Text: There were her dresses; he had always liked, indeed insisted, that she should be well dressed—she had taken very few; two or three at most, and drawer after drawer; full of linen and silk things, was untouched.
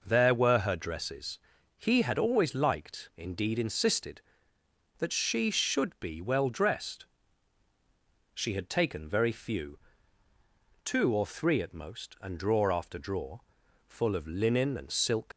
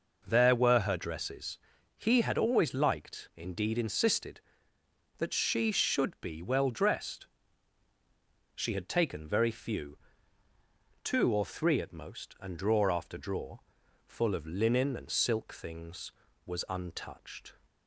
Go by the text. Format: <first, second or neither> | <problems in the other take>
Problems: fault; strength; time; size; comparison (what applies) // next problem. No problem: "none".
second | stops before "things was untouched"; at 15.3 s